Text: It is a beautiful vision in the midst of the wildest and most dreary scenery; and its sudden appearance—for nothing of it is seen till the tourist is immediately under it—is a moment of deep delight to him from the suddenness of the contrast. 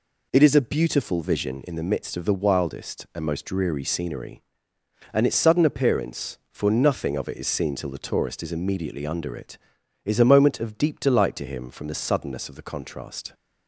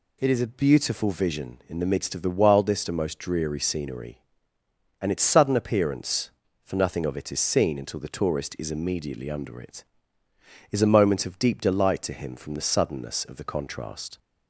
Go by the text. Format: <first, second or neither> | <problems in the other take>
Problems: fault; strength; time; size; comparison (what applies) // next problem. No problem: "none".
first | says "until" for "till"; at 7.7 s